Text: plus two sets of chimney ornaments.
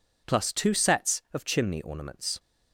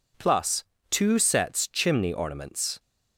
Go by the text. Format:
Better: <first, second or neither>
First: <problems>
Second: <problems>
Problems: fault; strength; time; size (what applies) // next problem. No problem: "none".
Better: first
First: none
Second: pauses between "plus" and "two"; slight; at 0.6 s; 0.26 s long // skips "of"; at 1.6 s